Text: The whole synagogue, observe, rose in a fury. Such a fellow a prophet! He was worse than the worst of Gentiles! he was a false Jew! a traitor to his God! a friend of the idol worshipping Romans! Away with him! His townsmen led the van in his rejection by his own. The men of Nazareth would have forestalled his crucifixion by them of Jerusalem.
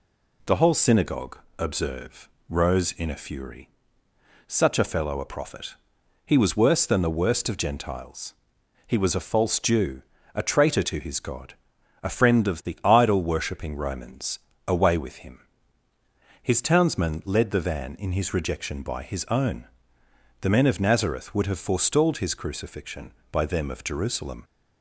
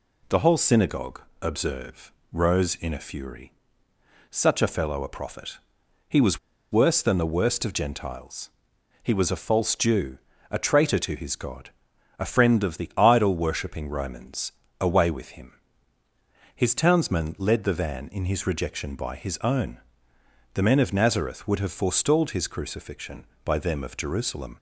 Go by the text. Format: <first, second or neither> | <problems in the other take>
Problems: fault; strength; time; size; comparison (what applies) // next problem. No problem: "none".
first | pauses between "was" and "worse"; slight; at 6.3 s; 0.34 s long